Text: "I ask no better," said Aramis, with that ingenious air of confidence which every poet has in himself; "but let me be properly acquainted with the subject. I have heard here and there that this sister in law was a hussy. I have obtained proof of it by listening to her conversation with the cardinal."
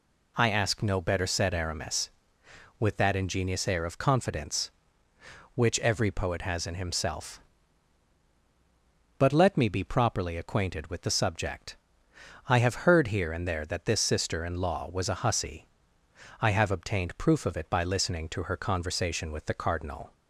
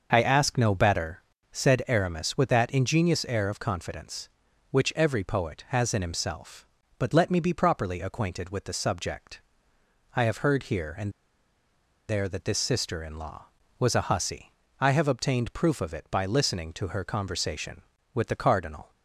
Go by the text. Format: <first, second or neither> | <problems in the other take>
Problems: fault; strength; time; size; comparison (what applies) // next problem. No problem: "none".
first | starts louder than the rest; until 1.1 s; 6.5 dB // pauses between "and" and "there"; at 11.1 s; 0.98 s long